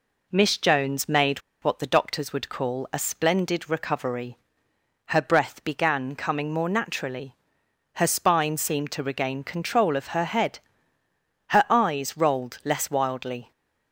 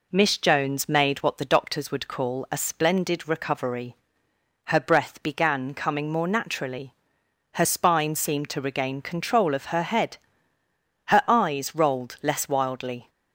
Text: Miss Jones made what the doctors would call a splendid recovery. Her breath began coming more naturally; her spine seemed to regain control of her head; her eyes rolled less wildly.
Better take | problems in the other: second | pauses between "made" and "what"; slight; at 1.3 s; 0.23 s long

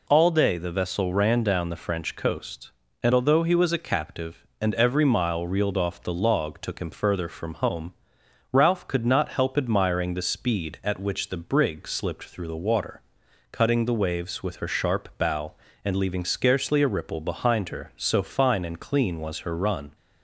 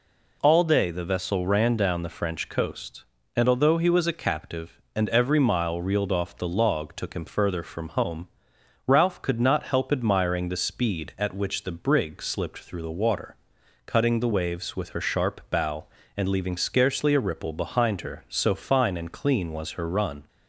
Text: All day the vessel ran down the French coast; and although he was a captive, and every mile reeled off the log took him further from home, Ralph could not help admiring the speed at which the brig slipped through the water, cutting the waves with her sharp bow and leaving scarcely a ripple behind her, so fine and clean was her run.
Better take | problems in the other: neither | none

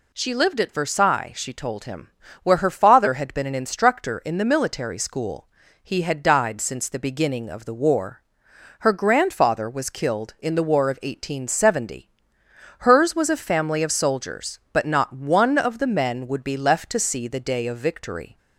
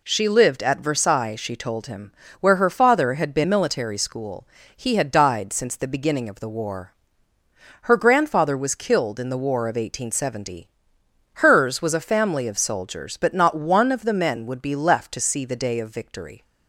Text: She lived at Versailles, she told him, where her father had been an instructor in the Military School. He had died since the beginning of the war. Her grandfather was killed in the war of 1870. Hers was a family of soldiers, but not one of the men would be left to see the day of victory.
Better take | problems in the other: first | skips "an instructor in the"; at 3.4 s

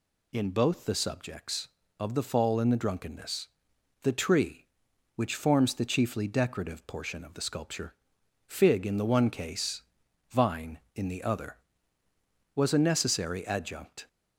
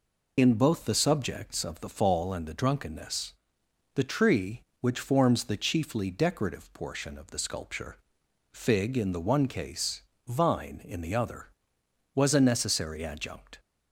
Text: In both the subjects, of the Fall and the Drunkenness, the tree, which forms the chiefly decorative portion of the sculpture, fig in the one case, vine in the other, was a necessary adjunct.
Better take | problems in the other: first | loses the start of "In"; at 0.3 s; 45 ms

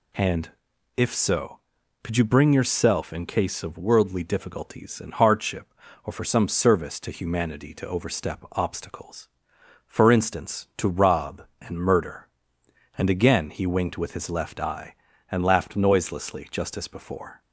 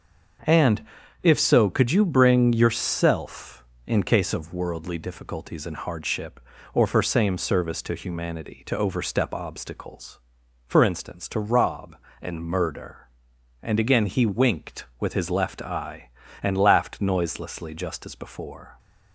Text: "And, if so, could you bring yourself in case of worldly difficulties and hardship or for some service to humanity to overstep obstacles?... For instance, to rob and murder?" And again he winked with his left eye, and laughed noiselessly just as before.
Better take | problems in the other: first | starts louder than the rest; until 1.8 s; 6.5 dB // says "same" for "some"; at 7.0 s

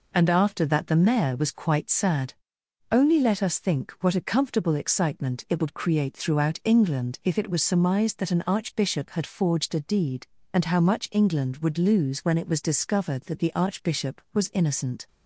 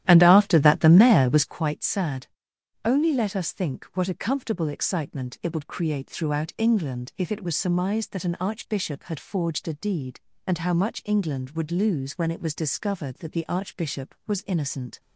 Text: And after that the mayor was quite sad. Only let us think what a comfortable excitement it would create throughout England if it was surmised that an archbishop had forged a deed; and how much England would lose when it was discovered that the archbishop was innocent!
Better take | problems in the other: first | starts louder than the rest; strong; until 1.6 s; 12.5 dB

